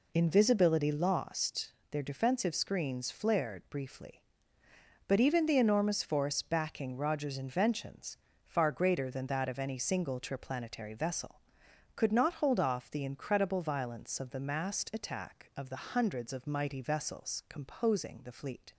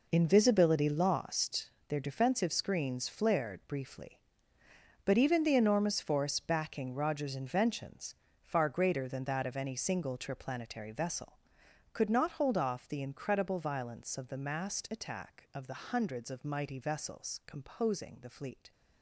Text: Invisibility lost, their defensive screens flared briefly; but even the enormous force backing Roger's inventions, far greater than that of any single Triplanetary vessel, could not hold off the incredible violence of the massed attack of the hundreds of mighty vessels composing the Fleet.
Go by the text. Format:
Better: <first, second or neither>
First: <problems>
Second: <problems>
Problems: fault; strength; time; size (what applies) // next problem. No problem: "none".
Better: first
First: none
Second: gets quieter; strong; throughout; 12 dB